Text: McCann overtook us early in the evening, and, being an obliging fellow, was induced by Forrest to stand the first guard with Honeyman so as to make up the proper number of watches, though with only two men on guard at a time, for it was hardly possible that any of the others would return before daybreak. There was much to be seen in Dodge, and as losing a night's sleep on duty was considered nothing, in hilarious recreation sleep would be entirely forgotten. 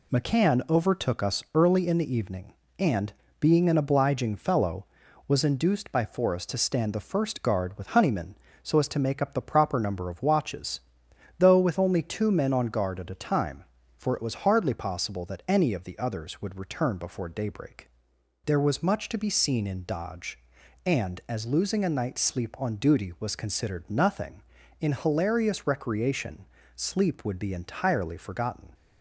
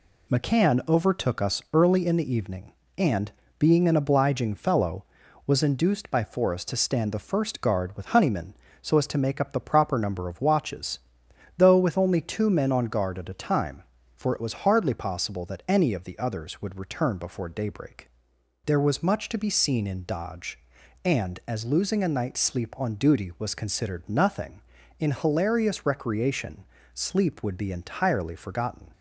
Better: neither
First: pauses between "recreation" and "sleep"; slight; at 26.4 s; 0.30 s long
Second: pauses between "recreation" and "sleep"; slight; at 26.6 s; 0.29 s long

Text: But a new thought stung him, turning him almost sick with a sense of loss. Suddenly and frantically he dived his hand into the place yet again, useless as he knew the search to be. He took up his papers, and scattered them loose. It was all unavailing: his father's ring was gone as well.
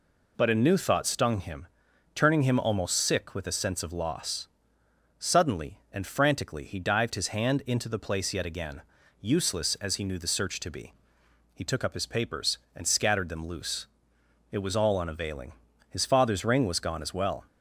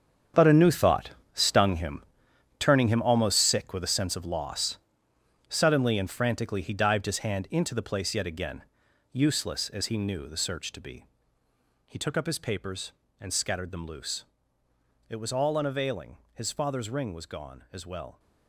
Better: first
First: none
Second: gets quieter; strong; throughout; 13 dB // pauses between "thought" and "stung"; slight; at 1.1 s; 0.22 s long

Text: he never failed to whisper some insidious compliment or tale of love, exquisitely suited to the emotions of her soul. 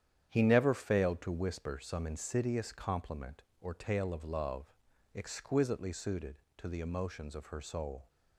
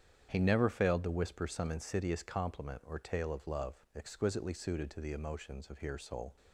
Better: first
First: starts louder than the rest; strong; until 1.3 s; 9.5 dB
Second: starts louder than the rest; strong; until 1.3 s; 8.5 dB // says "here" for "her"; at 5.7 s

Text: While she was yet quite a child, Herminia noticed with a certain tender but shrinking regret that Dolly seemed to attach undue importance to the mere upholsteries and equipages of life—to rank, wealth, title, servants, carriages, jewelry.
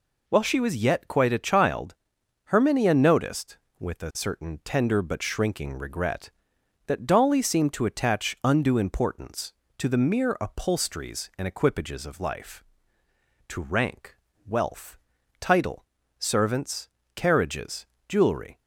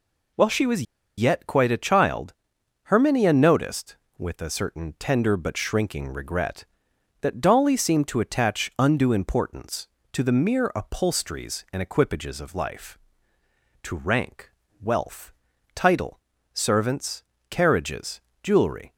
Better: first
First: none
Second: pauses between "was" and "yet"; slight; at 0.8 s; 0.35 s long

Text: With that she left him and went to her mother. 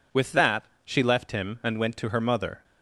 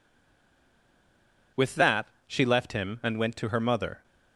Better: first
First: pauses between "that" and "she"; slight; at 0.6 s; 0.20 s long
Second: stays silent before the first word; noticeable; until 1.5 s; 1.5 s long // pauses between "that" and "she"; slight; at 2.0 s; 0.19 s long

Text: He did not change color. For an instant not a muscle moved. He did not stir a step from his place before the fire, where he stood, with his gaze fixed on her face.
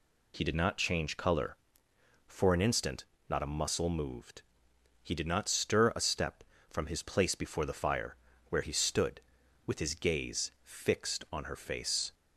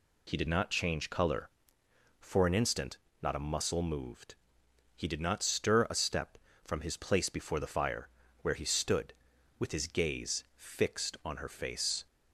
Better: neither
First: pauses between "instant" and "not"; slight; at 3.0 s; 0.24 s long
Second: pauses between "instant" and "not"; slight; at 2.9 s; 0.24 s long

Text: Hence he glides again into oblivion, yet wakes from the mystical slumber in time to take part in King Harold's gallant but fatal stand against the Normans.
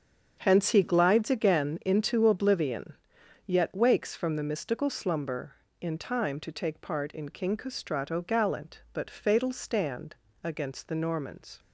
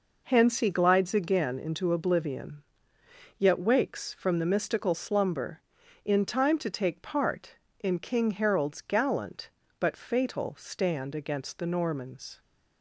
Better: second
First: starts louder than the rest; strong; until 1.3 s; 7.5 dB // says "Castrato" for "Harold's"; at 7.5 s // pauses between "stand" and "against"; slight; at 10.1 s; 0.26 s long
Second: none

